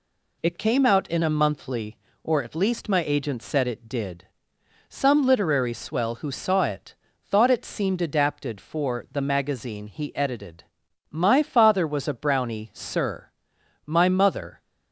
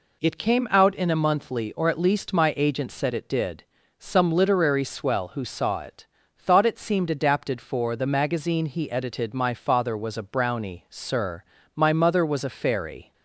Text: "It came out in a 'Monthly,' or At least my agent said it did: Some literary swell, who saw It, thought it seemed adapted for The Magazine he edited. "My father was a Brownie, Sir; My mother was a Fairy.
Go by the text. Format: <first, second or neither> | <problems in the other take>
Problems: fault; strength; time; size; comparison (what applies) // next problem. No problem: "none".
second | stops before "was a Fairy"; at 14.6 s